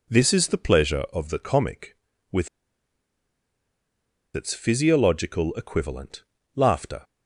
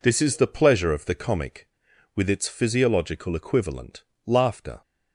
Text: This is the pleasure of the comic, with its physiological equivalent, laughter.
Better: second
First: pauses between "with" and "its"; strong; at 2.4 s; 1.8 s long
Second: none

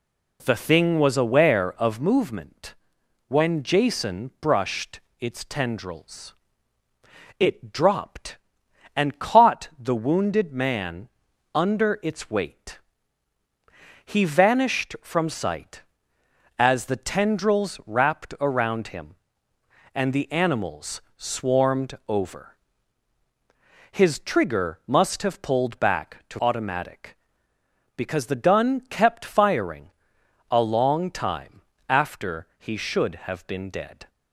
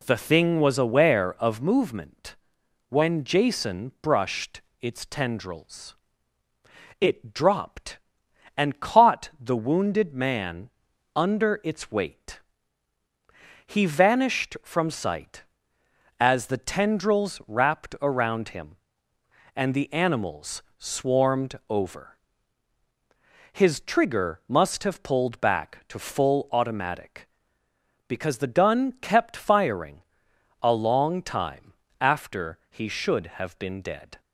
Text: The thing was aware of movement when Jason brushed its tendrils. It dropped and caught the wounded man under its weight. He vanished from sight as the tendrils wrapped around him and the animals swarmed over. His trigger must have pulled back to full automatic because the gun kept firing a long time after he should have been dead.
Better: second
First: pauses between "movement" and "when"; noticeable; at 2.7 s; 0.54 s long // pauses between "brushed" and "its"; slight; at 4.9 s; 0.20 s long // pauses between "man" and "under"; at 11.0 s; 0.44 s long // skips "full"; at 26.3 s // pauses between "firing" and "a"; noticeable; at 29.8 s; 0.62 s long // pauses between "time" and "after"; slight; at 31.6 s; 0.28 s long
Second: pauses between "movement" and "when"; noticeable; at 2.3 s; 0.54 s long // pauses between "brushed" and "its"; slight; at 4.6 s; 0.20 s long // pauses between "man" and "under"; at 10.7 s; 0.44 s long // pauses between "firing" and "a"; noticeable; at 30.0 s; 0.62 s long // pauses between "time" and "after"; slight; at 31.7 s; 0.28 s long

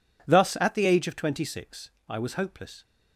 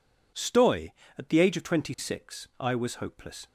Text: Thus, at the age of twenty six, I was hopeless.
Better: first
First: none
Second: says "Stoy" for "Thus"; at 0.3 s

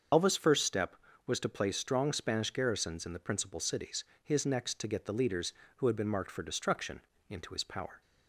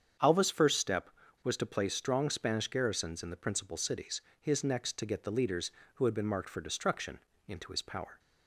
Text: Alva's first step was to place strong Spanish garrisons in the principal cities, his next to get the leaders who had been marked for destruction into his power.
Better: second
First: loses the start of "Alva's"; at 0.1 s; 65 ms // starts louder than the rest; until 1.4 s; 7 dB // pauses between "destruction" and "into"; slight; at 7.0 s; 0.28 s long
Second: starts louder than the rest; strong; until 1.5 s; 7.5 dB // pauses between "destruction" and "into"; slight; at 7.1 s; 0.28 s long

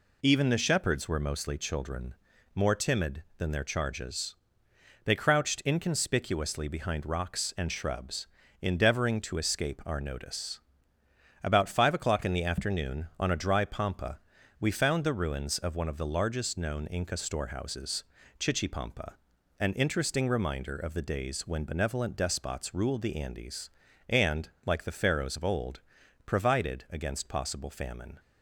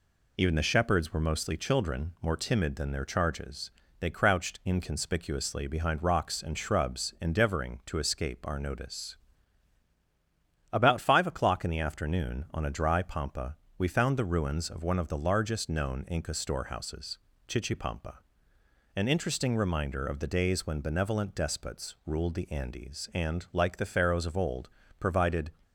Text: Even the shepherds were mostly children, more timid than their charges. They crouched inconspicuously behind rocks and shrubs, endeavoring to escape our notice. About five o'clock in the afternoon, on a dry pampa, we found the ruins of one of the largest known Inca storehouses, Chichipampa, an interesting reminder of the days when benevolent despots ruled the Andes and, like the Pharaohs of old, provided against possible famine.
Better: first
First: none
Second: stops before "against possible famine"; at 25.6 s

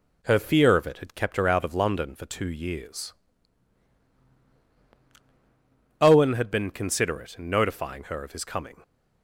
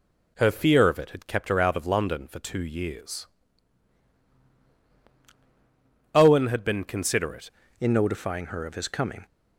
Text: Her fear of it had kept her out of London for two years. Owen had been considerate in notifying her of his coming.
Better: first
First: none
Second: changes voice at "in"; from 7.7 s on; 1.5 s long

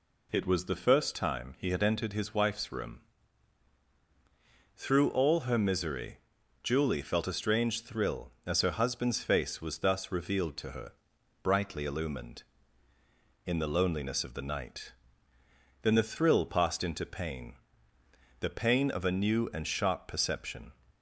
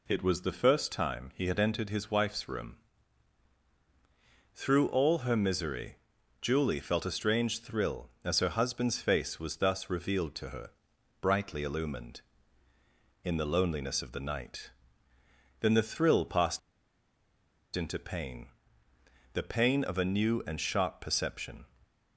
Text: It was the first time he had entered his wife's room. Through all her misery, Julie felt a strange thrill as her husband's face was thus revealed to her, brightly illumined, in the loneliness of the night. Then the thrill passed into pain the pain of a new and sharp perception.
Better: first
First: pauses between "pain" and "the"; noticeable; at 17.5 s; 0.86 s long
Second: pauses between "passed" and "into"; at 16.5 s; 1.1 s long // pauses between "pain" and "the"; noticeable; at 18.4 s; 0.86 s long

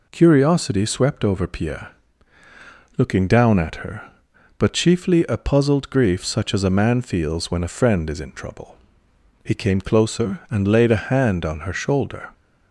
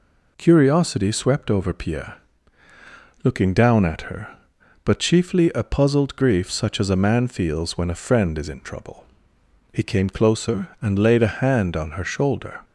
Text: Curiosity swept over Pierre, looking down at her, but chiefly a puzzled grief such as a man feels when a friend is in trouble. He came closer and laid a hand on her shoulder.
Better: neither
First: none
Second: none

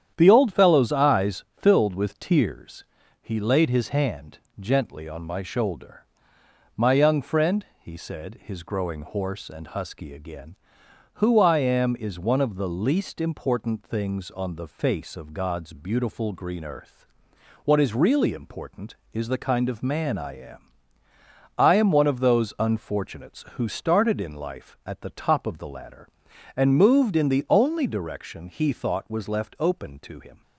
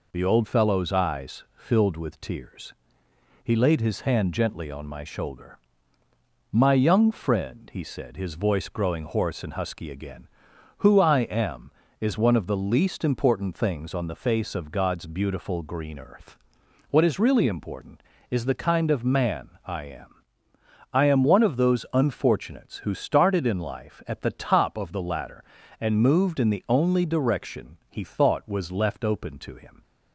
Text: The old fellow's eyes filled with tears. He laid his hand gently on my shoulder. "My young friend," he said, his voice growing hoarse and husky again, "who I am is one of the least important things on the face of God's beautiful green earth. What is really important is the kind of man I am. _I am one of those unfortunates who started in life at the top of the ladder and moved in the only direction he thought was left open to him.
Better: second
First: starts louder than the rest; strong; until 1.1 s; 9.5 dB // pauses between "hand" and "gently"; slight; at 4.3 s; 0.22 s long // skips "voice"; at 8.6 s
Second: none

